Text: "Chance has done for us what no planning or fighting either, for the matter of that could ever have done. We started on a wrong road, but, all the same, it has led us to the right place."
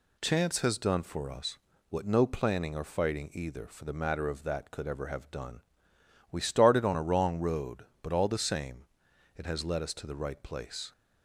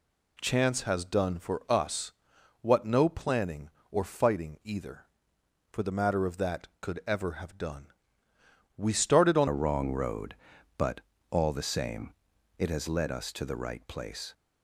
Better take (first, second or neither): first